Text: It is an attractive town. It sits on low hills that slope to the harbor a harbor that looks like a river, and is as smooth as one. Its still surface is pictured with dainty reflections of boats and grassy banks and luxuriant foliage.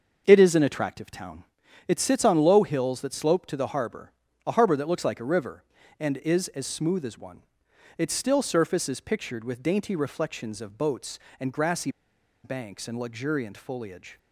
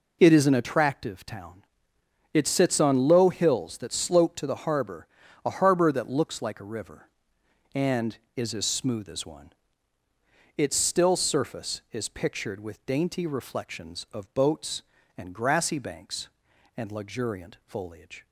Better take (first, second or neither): second